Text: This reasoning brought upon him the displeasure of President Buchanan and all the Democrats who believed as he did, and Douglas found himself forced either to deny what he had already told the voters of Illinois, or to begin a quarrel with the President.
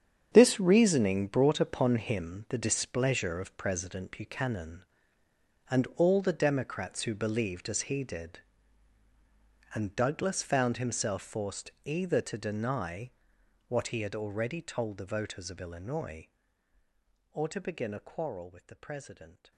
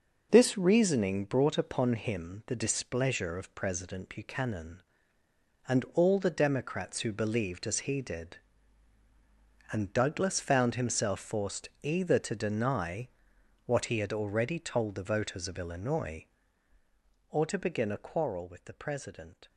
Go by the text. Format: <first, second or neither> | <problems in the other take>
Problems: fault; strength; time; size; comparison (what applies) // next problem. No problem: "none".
second | gets quieter; strong; throughout; 12.5 dB // pauses between "deny" and "what"; noticeable; at 13.1 s; 0.58 s long; noticeable in the second